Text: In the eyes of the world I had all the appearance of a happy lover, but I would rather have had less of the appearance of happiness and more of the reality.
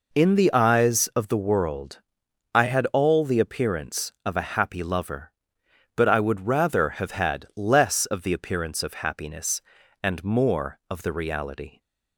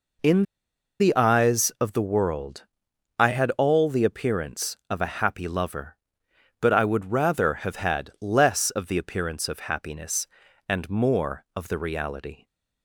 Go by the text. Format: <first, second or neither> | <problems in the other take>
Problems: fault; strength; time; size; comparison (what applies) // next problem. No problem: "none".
first | pauses between "In" and "the"; noticeable; at 0.4 s; 0.56 s long // pauses between "world" and "I"; noticeable; at 2.6 s; 0.56 s long; noticeable in the first